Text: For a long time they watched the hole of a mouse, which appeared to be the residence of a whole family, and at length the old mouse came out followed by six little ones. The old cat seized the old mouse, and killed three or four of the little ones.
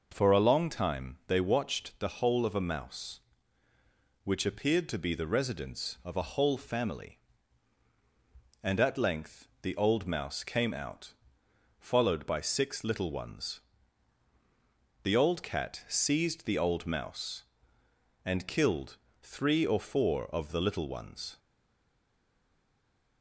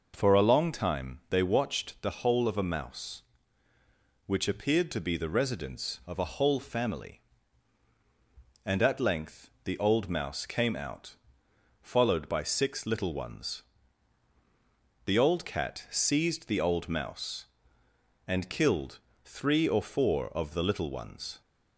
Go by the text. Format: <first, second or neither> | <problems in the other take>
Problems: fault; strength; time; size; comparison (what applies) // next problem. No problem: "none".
second | pauses between "length" and "the"; slight; at 9.4 s; 0.16 s long; slight in the second // pauses between "out" and "followed"; noticeable; at 11.1 s; 0.64 s long; noticeable in the second // pauses between "killed" and "three"; slight; at 18.9 s; 0.24 s long; slight in the second // stays silent after the last word; noticeable; from 21.3 s on; 1.9 s long